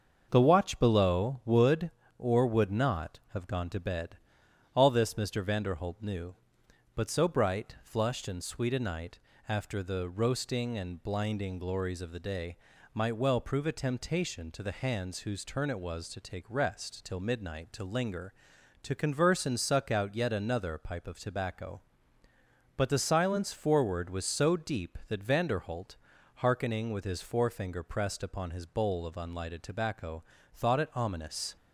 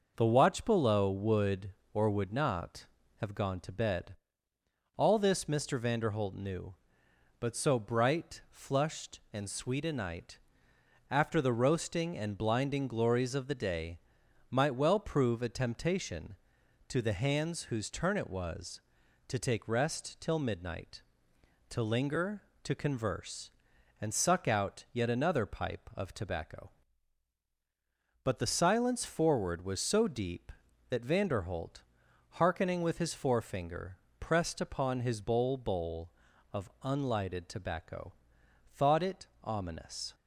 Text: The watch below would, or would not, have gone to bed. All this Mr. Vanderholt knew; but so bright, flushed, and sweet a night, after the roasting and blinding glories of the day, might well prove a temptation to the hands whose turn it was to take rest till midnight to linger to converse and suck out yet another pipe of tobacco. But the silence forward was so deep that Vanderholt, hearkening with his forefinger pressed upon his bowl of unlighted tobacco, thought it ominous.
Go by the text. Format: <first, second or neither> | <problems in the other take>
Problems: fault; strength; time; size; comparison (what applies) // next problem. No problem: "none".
first | starts louder than the rest; noticeable; until 1.1 s; 6 dB; also in the first // pauses between "forefinger" and "pressed"; slight; at 33.9 s; 0.24 s long // says "bowl" twice; at 35.5 s // pauses between "it" and "ominous"; slight; at 39.2 s; 0.16 s long